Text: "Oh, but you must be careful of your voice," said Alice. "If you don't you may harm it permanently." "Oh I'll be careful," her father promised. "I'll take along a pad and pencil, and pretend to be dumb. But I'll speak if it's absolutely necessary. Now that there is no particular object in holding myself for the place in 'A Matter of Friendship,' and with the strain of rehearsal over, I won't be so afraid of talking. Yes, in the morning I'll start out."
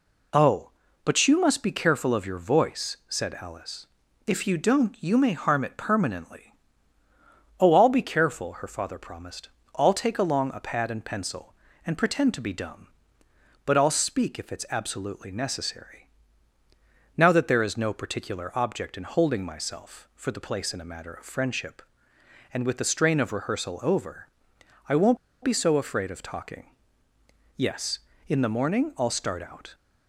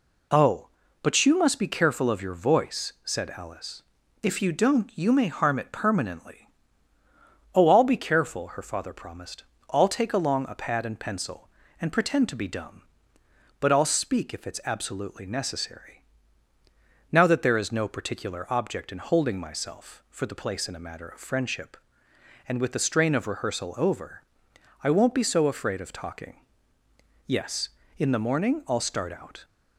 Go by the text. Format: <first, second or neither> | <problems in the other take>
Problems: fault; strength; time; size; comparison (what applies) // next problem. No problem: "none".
second | pauses between "won't" and "be"; slight; at 25.1 s; 0.25 s long